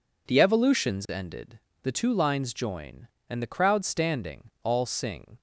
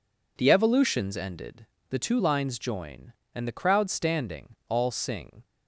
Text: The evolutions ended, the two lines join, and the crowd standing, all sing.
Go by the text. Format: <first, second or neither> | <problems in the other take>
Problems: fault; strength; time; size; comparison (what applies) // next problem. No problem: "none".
neither | none